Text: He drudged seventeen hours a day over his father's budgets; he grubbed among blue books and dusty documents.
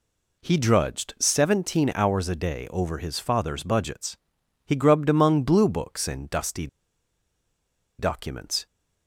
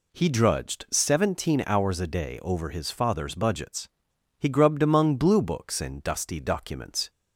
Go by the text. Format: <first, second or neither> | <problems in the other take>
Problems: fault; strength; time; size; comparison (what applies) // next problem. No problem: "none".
second | pauses between "dusty" and "documents"; strong; at 6.6 s; 1.3 s long